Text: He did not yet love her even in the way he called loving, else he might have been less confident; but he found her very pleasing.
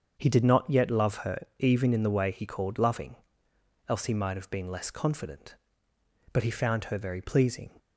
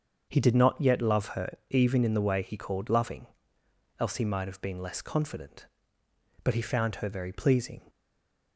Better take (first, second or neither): first